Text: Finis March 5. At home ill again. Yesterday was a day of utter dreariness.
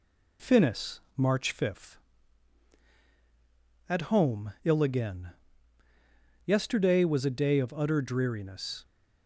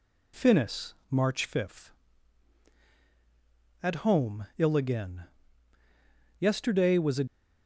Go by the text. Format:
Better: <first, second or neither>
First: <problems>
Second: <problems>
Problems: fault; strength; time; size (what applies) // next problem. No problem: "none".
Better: first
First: pauses between "Finis" and "March"; slight; at 1.0 s; 0.16 s long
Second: pauses between "Finis" and "March"; slight; at 0.9 s; 0.16 s long // stops before "day of utter dreariness"; at 7.2 s